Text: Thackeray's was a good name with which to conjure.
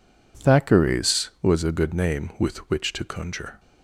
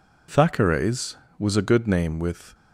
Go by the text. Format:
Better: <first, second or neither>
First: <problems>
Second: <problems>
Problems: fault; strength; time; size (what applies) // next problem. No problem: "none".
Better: first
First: none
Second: stops before "which to conjure"; at 2.5 s